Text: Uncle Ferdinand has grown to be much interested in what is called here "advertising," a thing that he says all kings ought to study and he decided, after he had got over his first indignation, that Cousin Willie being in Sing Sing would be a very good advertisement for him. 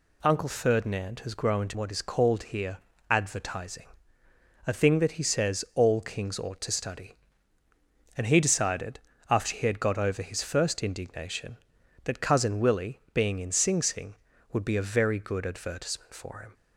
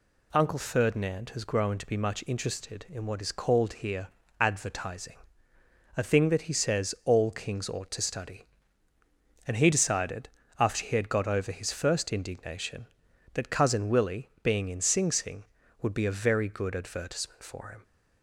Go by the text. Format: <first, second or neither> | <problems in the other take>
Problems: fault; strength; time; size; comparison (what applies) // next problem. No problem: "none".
second | skips "be much interested in"; at 1.7 s // pauses between "here" and "advertising"; slight; at 2.7 s; 0.32 s long; slight in the second